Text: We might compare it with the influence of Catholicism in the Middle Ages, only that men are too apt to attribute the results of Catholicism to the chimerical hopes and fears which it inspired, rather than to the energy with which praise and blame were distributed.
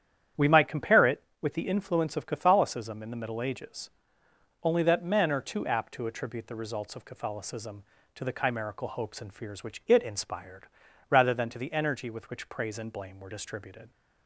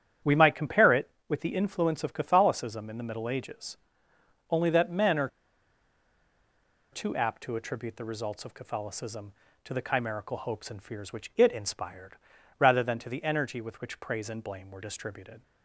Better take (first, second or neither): first